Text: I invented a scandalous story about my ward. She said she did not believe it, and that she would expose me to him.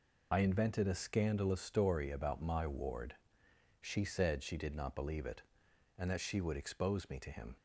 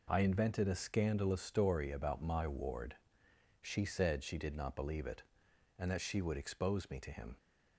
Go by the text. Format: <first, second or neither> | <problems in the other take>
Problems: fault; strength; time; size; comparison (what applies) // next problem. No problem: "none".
second | loses the start of "I"; at 0.3 s; 45 ms